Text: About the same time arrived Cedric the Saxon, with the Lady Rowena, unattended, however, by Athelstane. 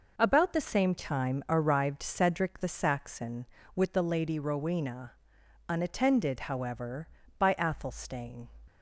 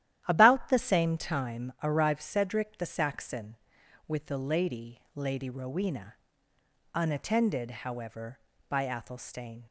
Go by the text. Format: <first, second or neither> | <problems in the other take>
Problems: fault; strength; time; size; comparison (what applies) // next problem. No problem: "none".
first | starts louder than the rest; strong; until 1.2 s; 12 dB // says "Lady" twice; at 5.1 s